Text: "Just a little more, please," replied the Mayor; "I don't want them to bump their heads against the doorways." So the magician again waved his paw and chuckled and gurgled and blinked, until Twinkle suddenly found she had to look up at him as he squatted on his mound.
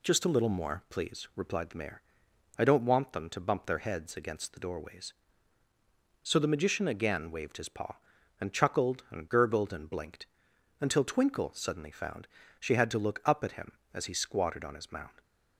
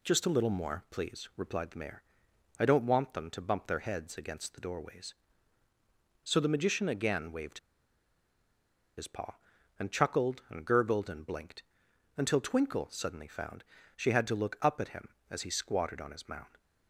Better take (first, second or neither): first